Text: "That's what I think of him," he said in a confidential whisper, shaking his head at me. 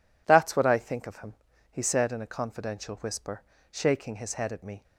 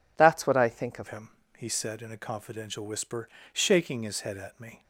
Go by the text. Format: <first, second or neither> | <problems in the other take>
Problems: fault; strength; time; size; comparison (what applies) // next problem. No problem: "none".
first | changes voice at "him"; from 1.0 s on; 3.8 s long